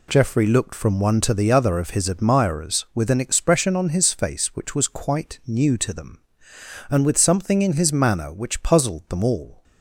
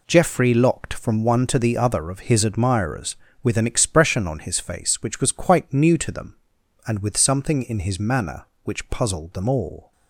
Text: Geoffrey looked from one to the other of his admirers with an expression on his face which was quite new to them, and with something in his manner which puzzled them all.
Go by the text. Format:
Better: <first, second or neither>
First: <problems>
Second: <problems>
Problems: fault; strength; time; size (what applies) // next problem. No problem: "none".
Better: first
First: none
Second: says "locked" for "looked"; at 0.5 s